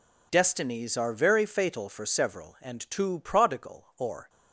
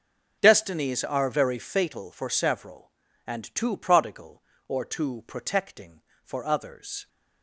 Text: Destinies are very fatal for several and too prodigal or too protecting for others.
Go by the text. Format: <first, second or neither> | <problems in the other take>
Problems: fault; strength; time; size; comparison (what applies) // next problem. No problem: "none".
second | stops before "too protecting for others"; at 4.2 s